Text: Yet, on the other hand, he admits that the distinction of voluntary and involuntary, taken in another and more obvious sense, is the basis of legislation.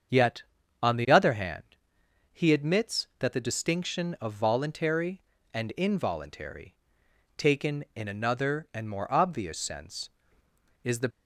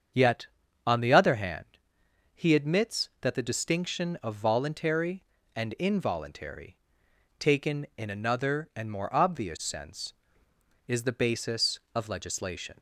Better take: second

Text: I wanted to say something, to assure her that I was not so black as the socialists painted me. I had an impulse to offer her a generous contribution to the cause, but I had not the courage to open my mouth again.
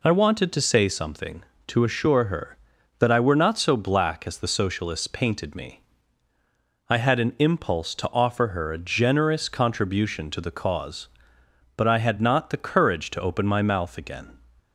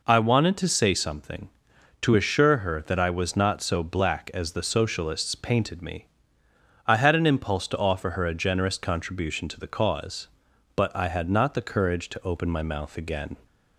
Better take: second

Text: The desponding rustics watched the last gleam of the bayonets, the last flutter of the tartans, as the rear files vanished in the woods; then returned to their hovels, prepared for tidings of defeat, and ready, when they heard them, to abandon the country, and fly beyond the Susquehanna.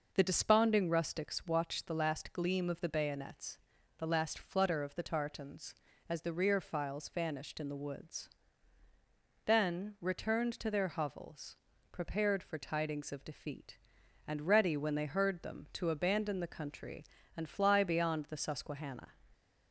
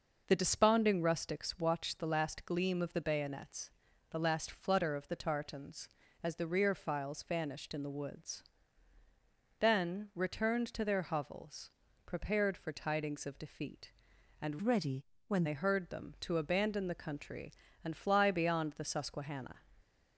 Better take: first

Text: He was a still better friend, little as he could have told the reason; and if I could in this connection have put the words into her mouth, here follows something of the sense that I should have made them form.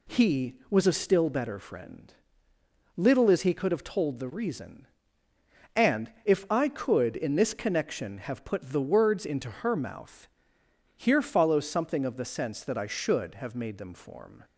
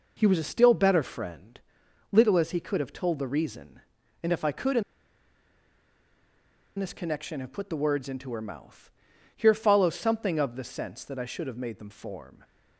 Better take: first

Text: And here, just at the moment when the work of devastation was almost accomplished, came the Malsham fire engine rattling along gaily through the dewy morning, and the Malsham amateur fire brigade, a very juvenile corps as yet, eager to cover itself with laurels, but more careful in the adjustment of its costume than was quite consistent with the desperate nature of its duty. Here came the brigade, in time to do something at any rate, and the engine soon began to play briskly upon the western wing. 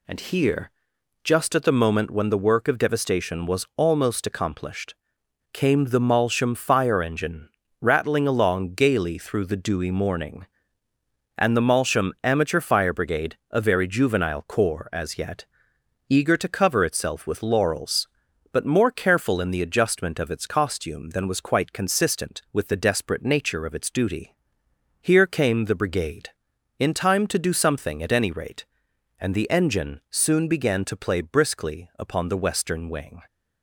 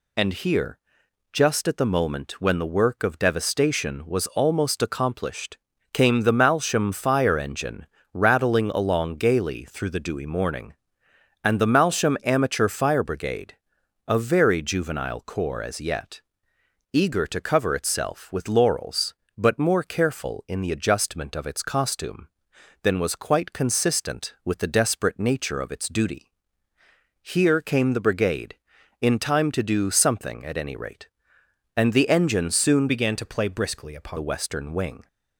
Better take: first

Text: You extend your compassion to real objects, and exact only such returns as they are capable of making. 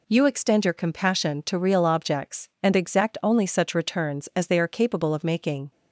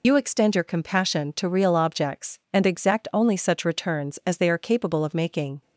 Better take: first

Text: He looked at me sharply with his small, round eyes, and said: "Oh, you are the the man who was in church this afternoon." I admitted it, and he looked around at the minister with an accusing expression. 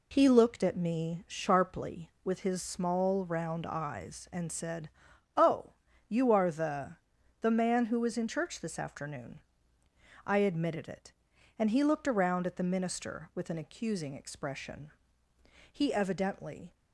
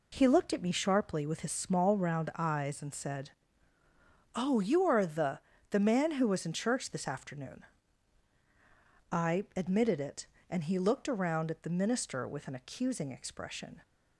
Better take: second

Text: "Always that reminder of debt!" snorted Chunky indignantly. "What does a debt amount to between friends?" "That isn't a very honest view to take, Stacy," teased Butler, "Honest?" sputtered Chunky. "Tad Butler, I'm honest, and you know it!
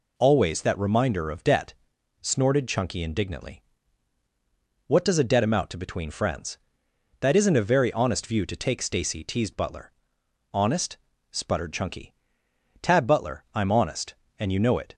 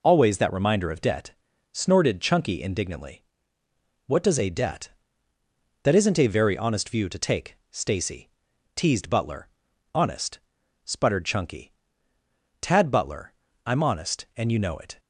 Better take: first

